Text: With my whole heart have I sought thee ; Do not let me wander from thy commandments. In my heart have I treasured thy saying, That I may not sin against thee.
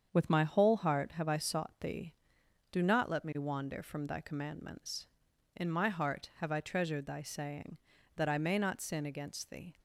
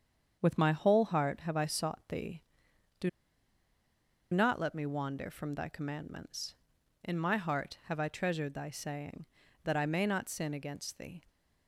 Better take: first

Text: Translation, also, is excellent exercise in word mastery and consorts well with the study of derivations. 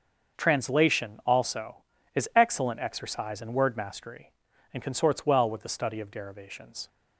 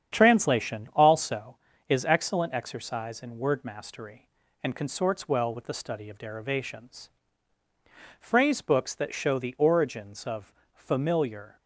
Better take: first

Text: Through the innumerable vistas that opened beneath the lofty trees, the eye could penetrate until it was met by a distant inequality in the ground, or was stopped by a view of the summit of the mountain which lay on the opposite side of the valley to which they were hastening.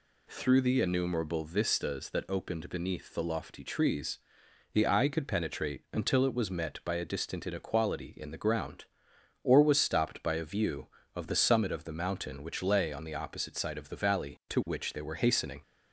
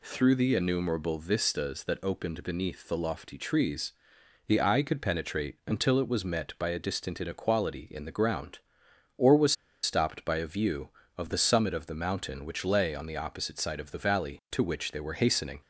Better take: first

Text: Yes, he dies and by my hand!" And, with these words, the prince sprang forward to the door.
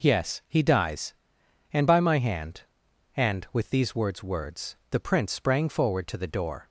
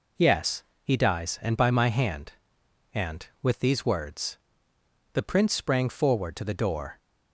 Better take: second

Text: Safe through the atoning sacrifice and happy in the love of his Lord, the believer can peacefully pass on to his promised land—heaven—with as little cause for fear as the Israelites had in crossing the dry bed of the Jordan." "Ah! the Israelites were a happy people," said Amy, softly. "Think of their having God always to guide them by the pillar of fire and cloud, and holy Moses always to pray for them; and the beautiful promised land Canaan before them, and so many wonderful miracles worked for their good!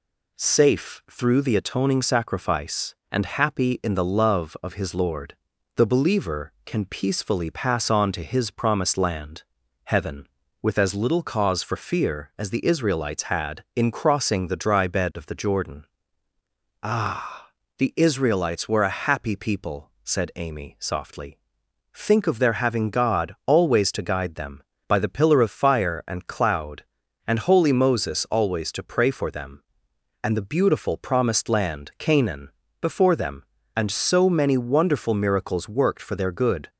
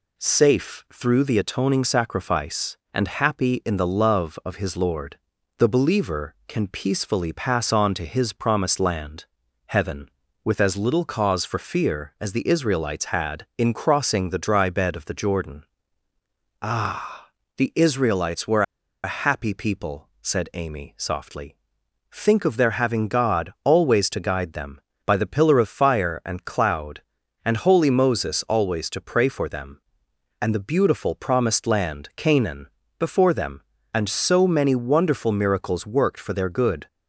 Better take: first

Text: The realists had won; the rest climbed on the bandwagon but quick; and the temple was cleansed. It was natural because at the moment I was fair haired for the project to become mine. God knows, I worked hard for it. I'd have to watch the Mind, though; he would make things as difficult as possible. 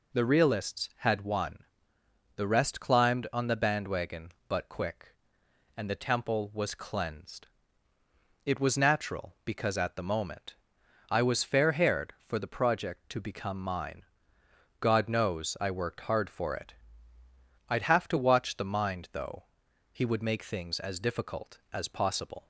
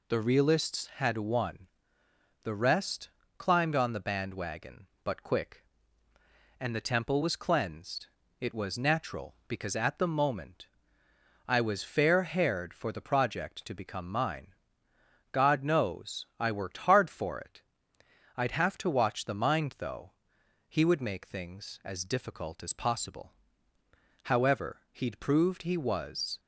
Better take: first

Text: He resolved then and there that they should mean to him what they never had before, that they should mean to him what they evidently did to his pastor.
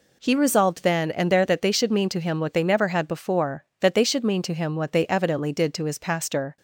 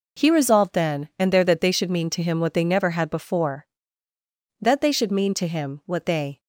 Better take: first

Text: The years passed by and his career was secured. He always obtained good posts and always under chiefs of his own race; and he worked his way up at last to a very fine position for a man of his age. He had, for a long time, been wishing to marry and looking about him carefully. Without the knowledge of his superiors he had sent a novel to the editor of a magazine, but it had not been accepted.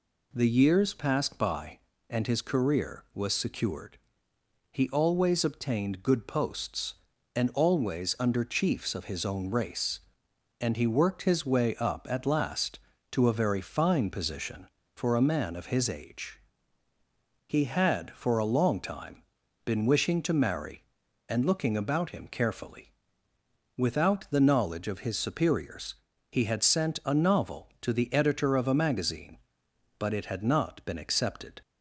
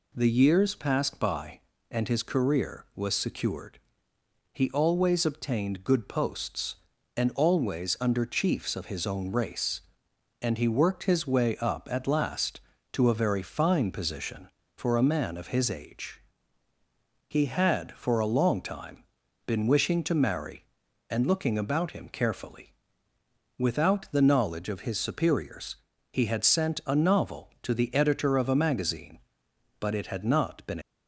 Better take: first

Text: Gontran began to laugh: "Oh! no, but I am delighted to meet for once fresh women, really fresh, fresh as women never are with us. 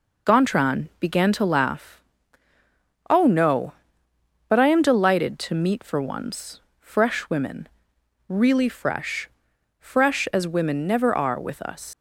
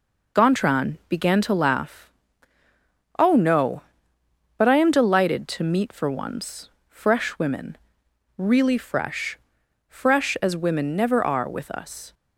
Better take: second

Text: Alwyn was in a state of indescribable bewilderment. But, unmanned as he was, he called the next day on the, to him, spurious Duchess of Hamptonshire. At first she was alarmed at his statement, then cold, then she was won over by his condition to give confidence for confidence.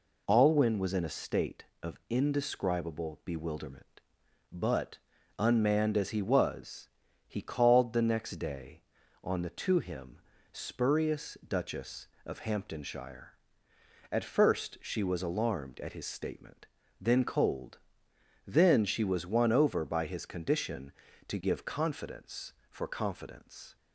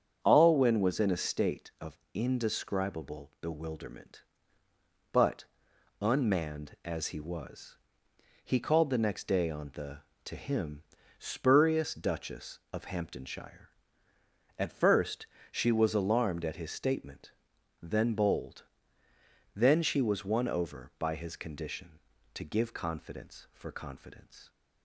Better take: first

